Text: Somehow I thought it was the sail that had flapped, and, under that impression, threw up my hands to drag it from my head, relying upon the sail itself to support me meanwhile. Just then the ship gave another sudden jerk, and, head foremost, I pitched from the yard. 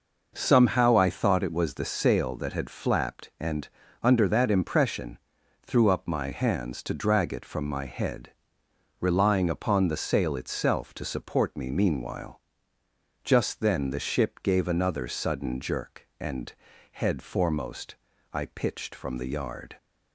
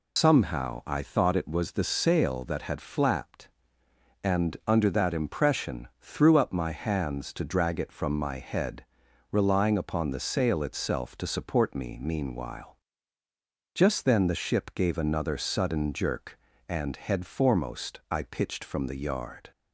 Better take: first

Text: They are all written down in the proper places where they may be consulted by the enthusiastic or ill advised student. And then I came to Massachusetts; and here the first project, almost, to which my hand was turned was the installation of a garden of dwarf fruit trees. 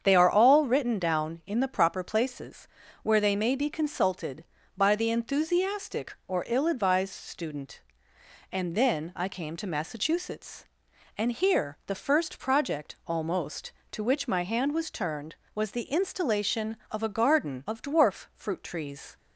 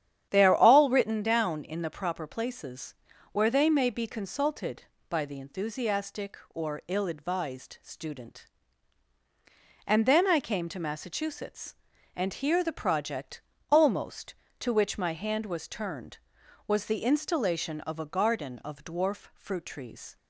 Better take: first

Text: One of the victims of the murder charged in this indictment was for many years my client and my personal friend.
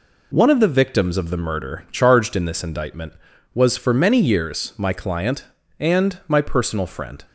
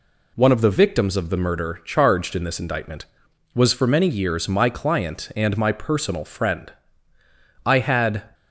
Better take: first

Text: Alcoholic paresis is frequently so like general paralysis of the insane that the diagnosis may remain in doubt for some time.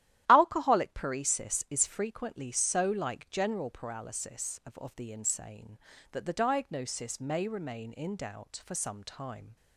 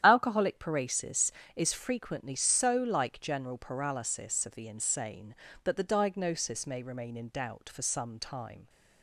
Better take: second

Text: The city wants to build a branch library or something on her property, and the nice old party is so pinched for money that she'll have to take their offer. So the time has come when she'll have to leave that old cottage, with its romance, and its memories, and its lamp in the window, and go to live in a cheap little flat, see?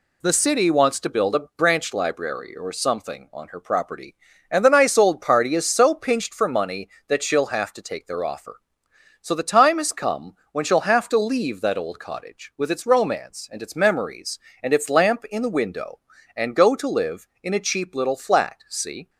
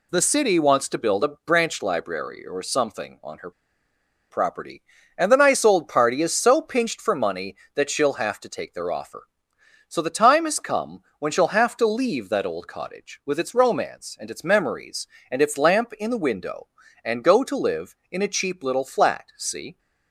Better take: first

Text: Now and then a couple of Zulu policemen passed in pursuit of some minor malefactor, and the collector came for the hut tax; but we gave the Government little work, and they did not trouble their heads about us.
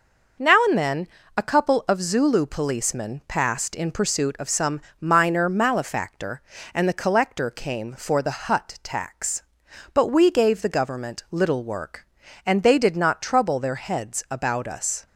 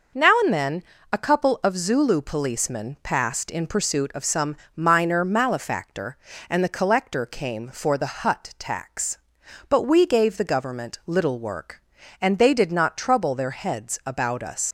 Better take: first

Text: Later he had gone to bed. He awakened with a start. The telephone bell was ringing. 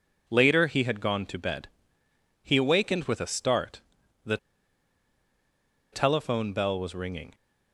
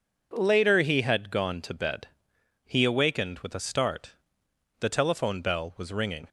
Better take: second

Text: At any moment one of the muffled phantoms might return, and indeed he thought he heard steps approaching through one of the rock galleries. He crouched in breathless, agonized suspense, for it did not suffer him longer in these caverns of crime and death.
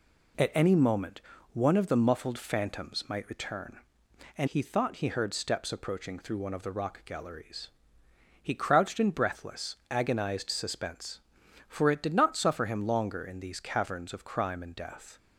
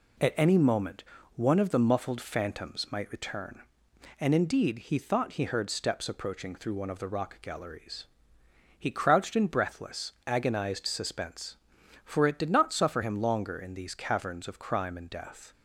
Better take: second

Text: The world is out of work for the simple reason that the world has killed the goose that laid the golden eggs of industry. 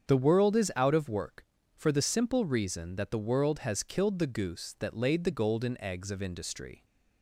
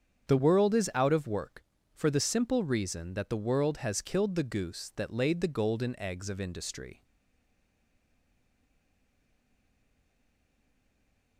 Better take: first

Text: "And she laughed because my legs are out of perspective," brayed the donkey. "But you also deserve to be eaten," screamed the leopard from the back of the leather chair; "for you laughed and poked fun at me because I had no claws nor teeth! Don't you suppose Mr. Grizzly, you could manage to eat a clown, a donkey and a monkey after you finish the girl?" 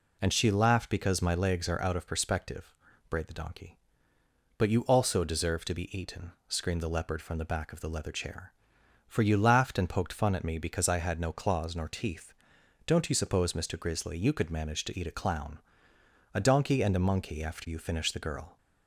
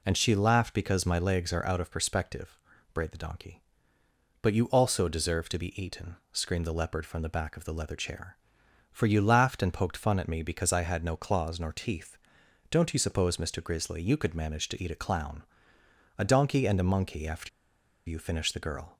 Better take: first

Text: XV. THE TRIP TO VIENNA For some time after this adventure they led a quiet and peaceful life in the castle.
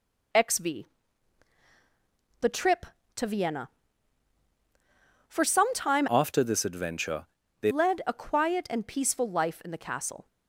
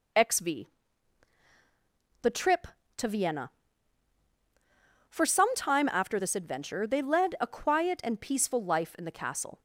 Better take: second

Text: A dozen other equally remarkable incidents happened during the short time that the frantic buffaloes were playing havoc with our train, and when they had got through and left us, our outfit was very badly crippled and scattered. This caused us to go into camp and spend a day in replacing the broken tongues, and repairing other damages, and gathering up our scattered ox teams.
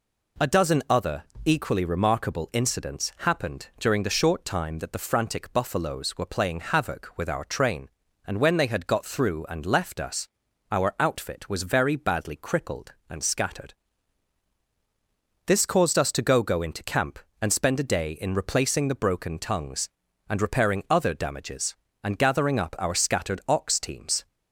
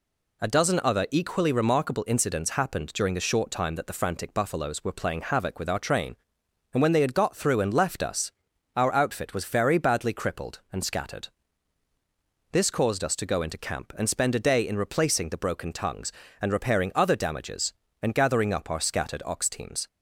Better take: second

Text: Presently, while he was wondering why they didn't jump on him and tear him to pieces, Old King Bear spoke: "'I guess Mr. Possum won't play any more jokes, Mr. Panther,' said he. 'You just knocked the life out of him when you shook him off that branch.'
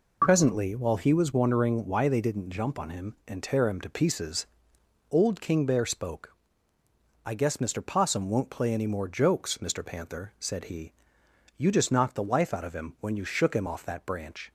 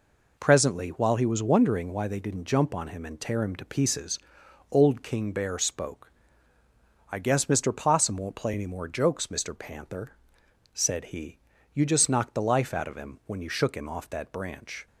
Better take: neither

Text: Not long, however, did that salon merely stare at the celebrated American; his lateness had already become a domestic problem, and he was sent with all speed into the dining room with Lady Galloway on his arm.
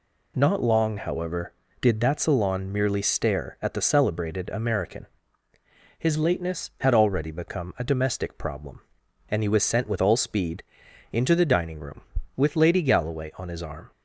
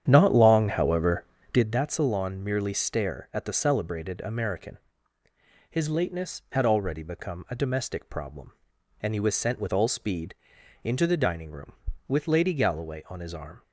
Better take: first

